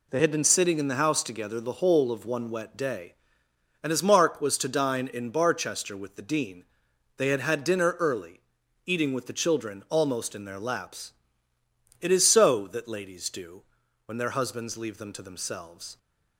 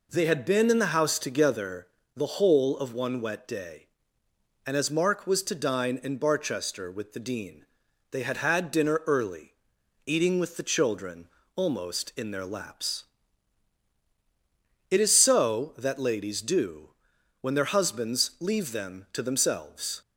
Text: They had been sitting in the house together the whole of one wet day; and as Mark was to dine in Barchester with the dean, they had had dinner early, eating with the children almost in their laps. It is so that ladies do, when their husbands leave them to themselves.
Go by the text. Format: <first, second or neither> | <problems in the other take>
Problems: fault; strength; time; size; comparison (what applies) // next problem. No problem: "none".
first | skips "sitting"; at 0.7 s // pauses between "together" and "the"; slight; at 1.8 s; 0.30 s long // pauses between "children" and "almost"; slight; at 11.2 s; 0.26 s long